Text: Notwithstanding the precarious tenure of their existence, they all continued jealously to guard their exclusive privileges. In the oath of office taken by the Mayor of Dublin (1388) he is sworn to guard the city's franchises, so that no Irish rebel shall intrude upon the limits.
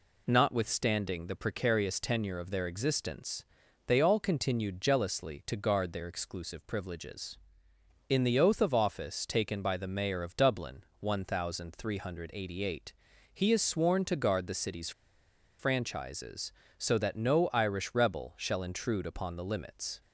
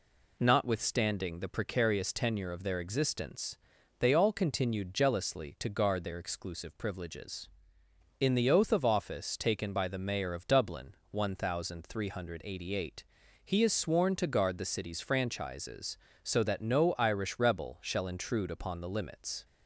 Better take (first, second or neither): second